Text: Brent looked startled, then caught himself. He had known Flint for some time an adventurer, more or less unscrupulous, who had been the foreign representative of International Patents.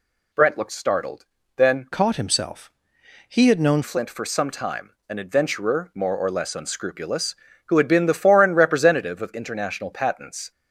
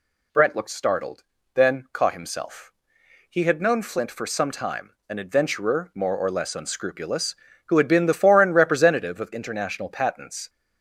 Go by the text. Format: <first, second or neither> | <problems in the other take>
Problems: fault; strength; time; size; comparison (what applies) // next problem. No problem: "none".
second | changes voice from "caught" to "known"; from 1.9 to 3.8 s; 1.9 s long // pauses between "time" and "an"; slight; at 4.9 s; 0.18 s long; slight in the second